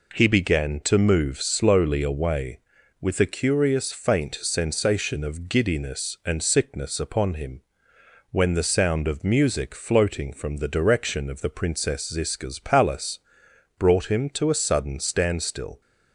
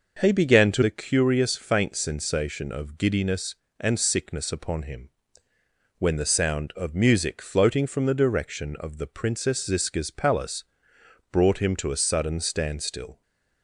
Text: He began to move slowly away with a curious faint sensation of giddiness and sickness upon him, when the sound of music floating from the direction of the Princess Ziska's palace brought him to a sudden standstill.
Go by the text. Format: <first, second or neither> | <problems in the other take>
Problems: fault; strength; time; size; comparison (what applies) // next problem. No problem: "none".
first | skips "move slowly away with"; at 0.8 s // pauses between "palace" and "brought"; noticeable; at 10.6 s; 0.66 s long; noticeable in the first // stays silent after the last word; slight; from 13.1 s on; 0.5 s long